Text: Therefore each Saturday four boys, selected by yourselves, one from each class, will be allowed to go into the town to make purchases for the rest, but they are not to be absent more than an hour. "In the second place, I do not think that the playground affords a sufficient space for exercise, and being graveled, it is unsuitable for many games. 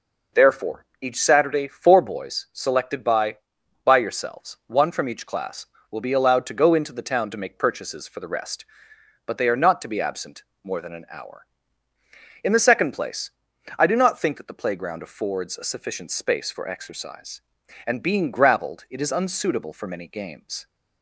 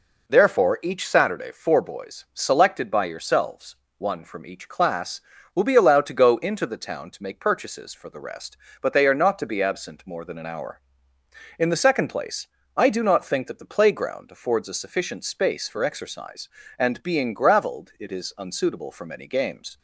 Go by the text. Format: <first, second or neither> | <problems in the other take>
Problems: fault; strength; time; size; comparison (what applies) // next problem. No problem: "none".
second | pauses between "Therefore" and "each"; slight; at 0.8 s; 0.16 s long // says "by" twice; at 3.8 s // pauses between "absent" and "more"; slight; at 10.4 s; 0.22 s long